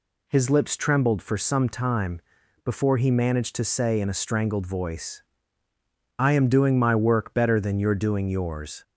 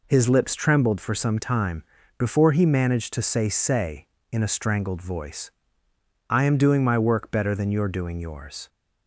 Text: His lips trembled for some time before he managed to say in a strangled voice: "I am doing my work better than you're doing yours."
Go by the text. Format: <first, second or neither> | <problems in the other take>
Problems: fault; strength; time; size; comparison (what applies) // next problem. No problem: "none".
first | pauses between "time" and "before"; slight; at 1.8 s; 0.36 s long; also in the first // says "say" twice; at 3.4 s